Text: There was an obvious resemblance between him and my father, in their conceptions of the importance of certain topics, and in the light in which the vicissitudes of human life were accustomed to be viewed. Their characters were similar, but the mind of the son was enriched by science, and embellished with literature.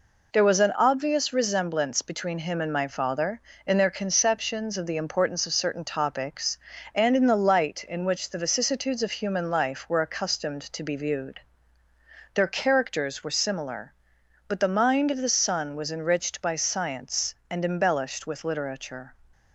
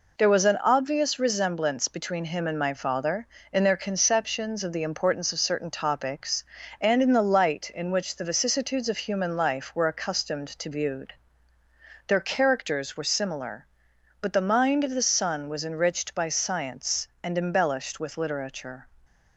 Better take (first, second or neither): first